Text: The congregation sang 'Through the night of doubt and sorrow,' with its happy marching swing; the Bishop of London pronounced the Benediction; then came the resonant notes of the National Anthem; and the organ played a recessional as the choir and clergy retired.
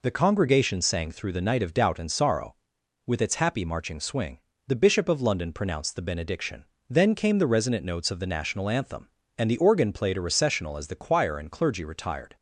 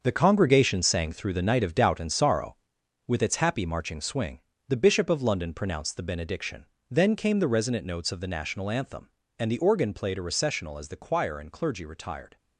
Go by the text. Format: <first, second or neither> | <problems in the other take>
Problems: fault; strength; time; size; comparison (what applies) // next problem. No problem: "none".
first | gets quieter; strong; throughout; 10 dB